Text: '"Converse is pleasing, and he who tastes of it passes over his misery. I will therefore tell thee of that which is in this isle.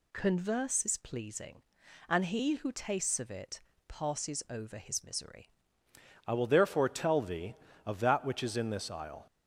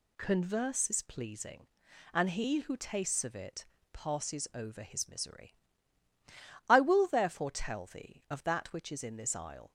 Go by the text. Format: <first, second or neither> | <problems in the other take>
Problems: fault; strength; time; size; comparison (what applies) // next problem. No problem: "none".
second | pauses between "it" and "passes"; slight; at 3.6 s; 0.26 s long; slight in the second // changes voice at "I"; from 6.2 s on; 3.0 s long